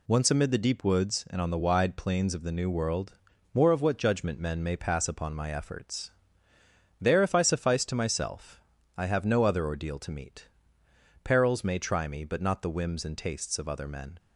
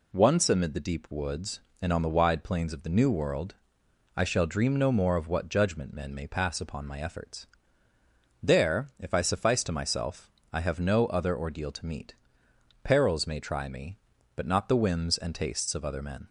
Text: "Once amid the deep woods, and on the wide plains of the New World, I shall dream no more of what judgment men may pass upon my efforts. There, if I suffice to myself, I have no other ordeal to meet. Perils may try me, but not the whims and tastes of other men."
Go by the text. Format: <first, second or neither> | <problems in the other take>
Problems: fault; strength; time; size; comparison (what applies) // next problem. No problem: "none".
second | skips "I shall dream no"; at 3.3 s